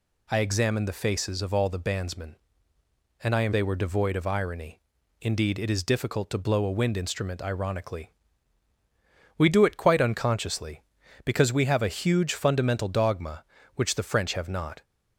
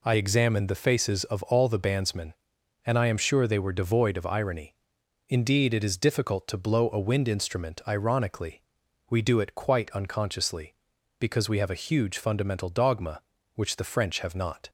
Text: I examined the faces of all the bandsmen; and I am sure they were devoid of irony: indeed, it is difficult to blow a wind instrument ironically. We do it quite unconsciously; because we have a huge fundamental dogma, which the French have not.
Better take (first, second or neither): second